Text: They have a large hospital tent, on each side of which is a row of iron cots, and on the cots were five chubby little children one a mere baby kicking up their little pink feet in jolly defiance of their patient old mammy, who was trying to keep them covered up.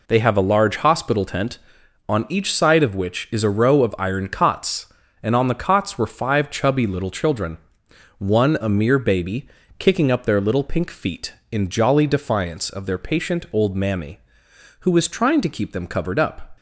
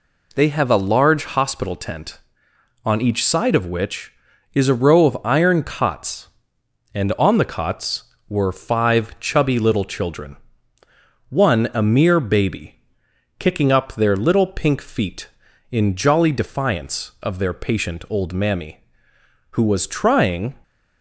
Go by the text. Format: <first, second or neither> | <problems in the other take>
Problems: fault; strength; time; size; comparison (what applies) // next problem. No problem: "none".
first | pauses between "children" and "one"; noticeable; at 10.3 s; 0.94 s long; noticeable in the first // pauses between "baby" and "kicking"; noticeable; at 12.7 s; 0.60 s long; slight in the first // stops before "to keep them covered up"; at 20.6 s